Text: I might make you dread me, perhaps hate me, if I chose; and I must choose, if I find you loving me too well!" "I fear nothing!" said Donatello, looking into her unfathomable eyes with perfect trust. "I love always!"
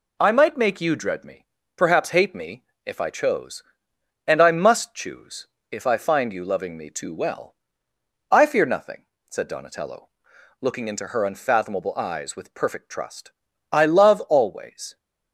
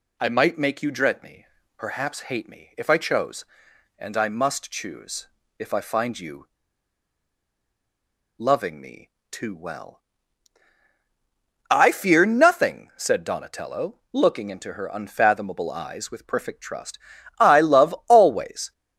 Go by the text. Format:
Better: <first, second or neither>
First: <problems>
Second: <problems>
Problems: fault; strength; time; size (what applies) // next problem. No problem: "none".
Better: first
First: none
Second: pauses between "you" and "loving"; strong; at 6.4 s; 1.9 s long // pauses between "me" and "too"; slight; at 9.0 s; 0.20 s long